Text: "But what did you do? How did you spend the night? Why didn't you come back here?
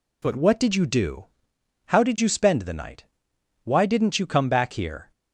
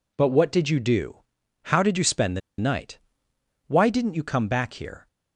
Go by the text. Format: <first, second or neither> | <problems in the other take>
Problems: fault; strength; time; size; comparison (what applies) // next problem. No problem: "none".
first | pauses between "the" and "night"; slight; at 2.4 s; 0.18 s long